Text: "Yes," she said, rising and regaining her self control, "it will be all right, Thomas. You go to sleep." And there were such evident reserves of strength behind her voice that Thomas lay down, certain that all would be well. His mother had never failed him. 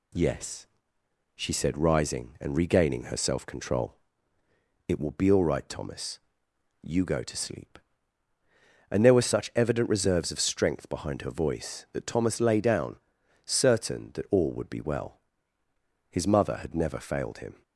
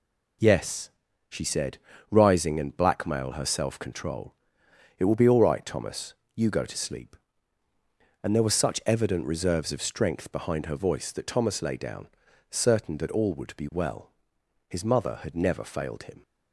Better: first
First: none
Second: says "blackmail" for "regaining"; at 2.7 s

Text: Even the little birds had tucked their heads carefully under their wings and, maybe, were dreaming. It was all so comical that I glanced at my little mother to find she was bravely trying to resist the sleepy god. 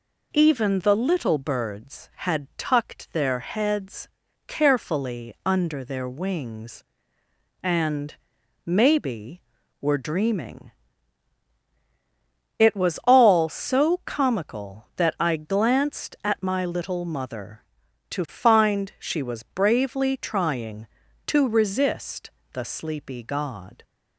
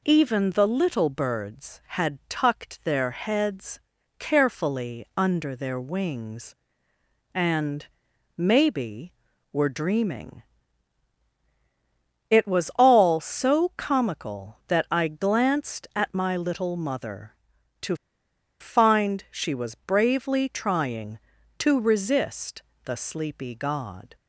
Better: first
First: pauses between "heads" and "carefully"; at 4.0 s; 0.40 s long // pauses between "resist" and "the"; slight; at 22.3 s; 0.22 s long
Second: pauses between "heads" and "carefully"; at 3.7 s; 0.40 s long // pauses between "to" and "find"; noticeable; at 17.9 s; 0.66 s long // pauses between "resist" and "the"; slight; at 22.6 s; 0.22 s long

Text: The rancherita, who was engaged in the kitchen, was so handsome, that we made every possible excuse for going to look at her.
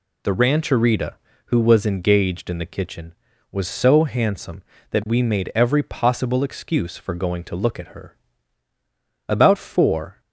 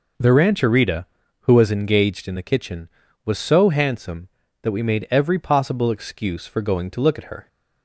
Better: second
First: goes on to say "About four"; noticeable; from 9.2 s on; 0.92 s long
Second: none

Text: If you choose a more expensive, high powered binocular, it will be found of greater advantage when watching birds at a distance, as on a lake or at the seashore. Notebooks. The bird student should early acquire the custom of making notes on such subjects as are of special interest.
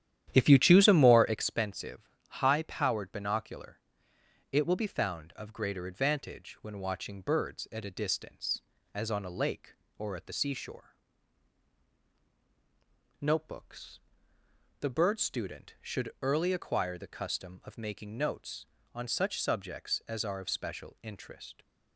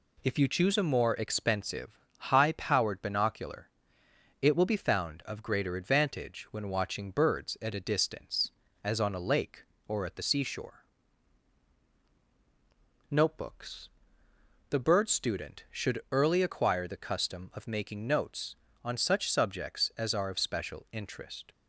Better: second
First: starts louder than the rest; strong; until 1.5 s; 11 dB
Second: none

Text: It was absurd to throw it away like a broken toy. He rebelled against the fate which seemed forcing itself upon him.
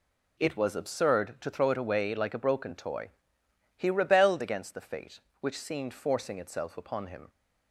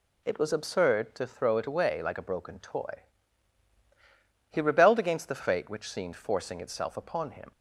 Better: neither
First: none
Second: none

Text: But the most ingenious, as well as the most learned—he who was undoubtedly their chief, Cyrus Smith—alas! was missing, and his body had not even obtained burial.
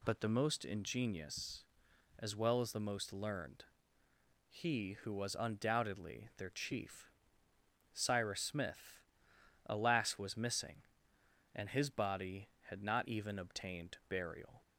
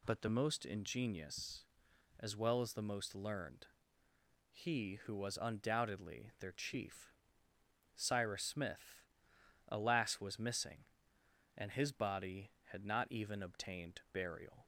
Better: neither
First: none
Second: none

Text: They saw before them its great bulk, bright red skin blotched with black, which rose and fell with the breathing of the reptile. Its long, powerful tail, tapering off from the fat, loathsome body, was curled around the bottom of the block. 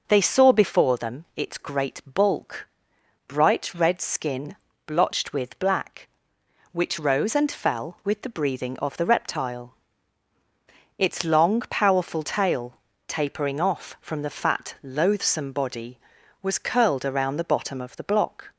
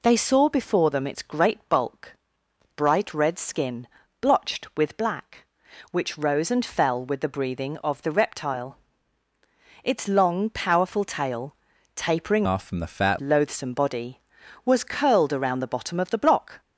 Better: first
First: pauses between "skin" and "blotched"; slight; at 4.5 s; 0.30 s long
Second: pauses between "skin" and "blotched"; slight; at 3.8 s; 0.34 s long // changes voice from "off" to "fat"; from 12.4 to 13.1 s; 0.7 s long

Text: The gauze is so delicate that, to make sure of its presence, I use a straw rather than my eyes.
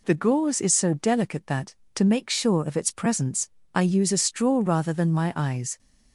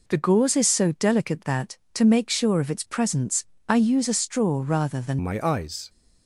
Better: first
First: none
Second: changes voice at "my"; from 5.2 s on; 0.6 s long

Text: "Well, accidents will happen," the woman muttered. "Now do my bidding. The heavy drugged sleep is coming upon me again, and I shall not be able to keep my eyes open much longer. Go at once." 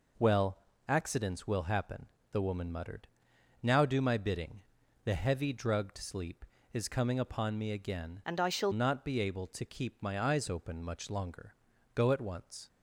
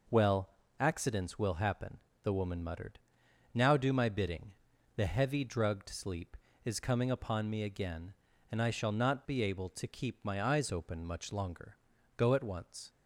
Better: second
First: changes voice from "and" to "shall"; from 8.2 to 8.7 s; 0.5 s long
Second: none

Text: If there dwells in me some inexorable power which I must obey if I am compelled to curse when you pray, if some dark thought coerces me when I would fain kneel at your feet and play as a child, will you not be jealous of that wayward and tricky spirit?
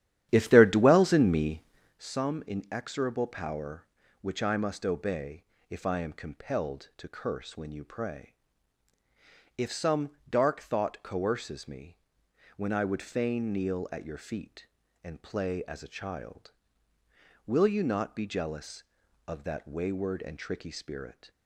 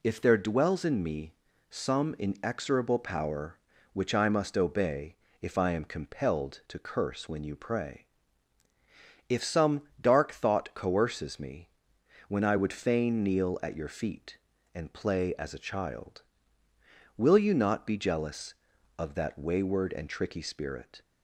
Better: second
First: starts louder than the rest; strong; until 2.0 s; 11 dB // pauses between "me" and "some"; slight; at 1.6 s; 0.36 s long // pauses between "obey" and "if"; slight; at 5.4 s; 0.24 s long // pauses between "some" and "dark"; slight; at 10.0 s; 0.18 s long // pauses between "me" and "when"; noticeable; at 11.9 s; 0.58 s long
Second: pauses between "me" and "some"; slight; at 1.3 s; 0.36 s long // pauses between "obey" and "if"; slight; at 5.1 s; 0.24 s long // pauses between "some" and "dark"; slight; at 9.8 s; 0.18 s long // pauses between "me" and "when"; noticeable; at 11.6 s; 0.58 s long

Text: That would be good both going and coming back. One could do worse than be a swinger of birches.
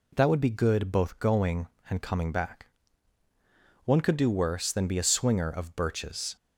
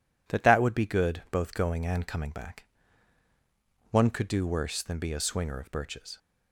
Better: first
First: none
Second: says "That" twice; at 0.4 s

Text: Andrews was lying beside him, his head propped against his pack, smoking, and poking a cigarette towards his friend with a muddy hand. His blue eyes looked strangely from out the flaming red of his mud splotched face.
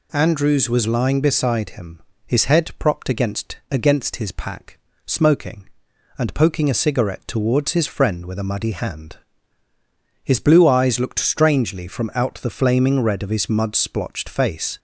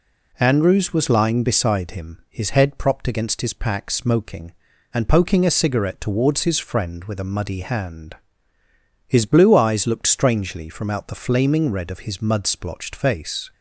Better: second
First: says "against" twice; at 3.7 s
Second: none

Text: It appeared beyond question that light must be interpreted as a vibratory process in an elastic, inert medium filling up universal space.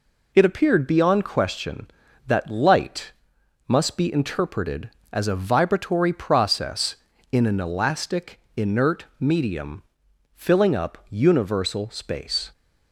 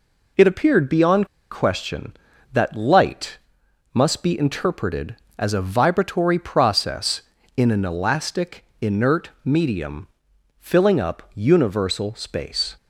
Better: first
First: pauses between "light" and "must"; noticeable; at 3.1 s; 0.54 s long // pauses between "medium" and "filling"; noticeable; at 9.8 s; 0.54 s long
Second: pauses between "beyond" and "question"; slight; at 1.2 s; 0.24 s long // pauses between "light" and "must"; noticeable; at 3.3 s; 0.54 s long // pauses between "medium" and "filling"; noticeable; at 10.0 s; 0.54 s long

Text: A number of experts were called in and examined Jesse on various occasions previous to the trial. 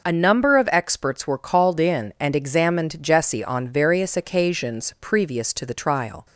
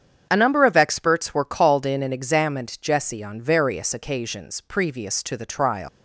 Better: first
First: none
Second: starts louder than the rest; strong; until 1.3 s; 8 dB // leaves "trial" unfinished; at 5.8 s; 115 ms

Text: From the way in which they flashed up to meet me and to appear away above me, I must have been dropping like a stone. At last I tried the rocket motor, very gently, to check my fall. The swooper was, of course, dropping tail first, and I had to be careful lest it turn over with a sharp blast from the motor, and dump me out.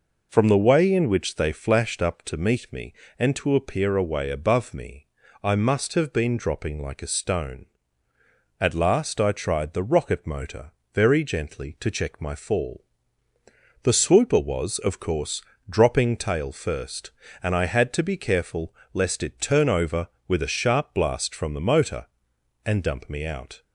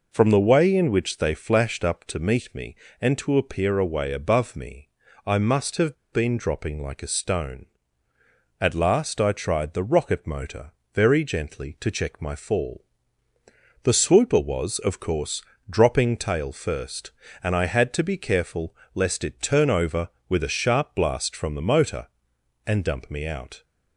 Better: first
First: pauses between "careful" and "lest"; slight; at 18.7 s; 0.18 s long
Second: pauses between "have" and "been"; slight; at 5.9 s; 0.18 s long // pauses between "careful" and "lest"; slight; at 18.7 s; 0.18 s long

